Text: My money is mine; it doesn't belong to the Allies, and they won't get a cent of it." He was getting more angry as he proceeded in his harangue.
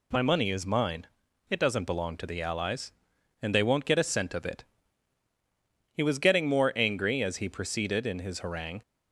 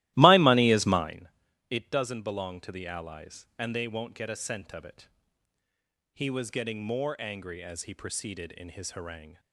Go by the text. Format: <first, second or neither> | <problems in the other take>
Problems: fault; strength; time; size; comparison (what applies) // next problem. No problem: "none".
first | starts louder than the rest; strong; until 1.2 s; 16.5 dB